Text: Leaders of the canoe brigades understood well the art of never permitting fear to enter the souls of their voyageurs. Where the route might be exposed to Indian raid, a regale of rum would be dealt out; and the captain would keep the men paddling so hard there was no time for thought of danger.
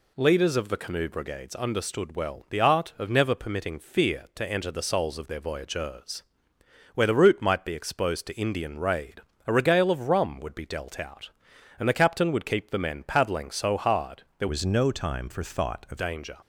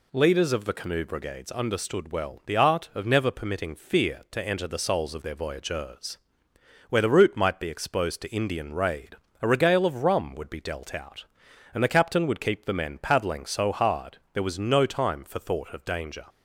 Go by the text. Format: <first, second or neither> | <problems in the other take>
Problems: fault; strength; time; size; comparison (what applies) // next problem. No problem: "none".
second | pauses between "hard" and "there"; slight; at 14.2 s; 0.16 s long; slight in the second // changes voice from "was" to "of"; from 14.4 to 15.9 s; 1.5 s long